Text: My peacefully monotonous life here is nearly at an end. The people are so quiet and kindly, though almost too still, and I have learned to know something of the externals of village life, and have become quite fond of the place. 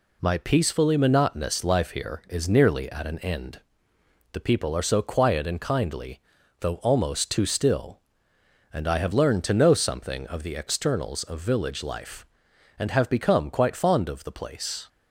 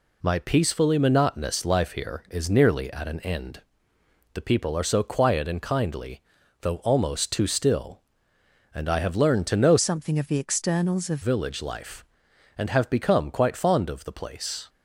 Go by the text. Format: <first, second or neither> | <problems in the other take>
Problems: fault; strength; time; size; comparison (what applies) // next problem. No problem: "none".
first | changes voice from "something" to "of"; from 9.7 to 11.2 s; 1.5 s long